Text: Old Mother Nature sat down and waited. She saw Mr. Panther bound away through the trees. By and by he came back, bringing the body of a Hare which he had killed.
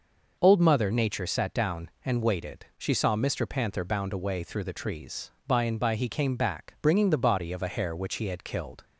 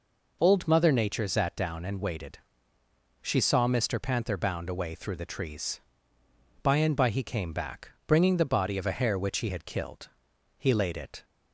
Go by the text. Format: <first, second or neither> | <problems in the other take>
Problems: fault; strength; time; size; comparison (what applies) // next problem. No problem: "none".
first | goes on to say "He laid it"; noticeable; from 10.5 s on; 0.66 s long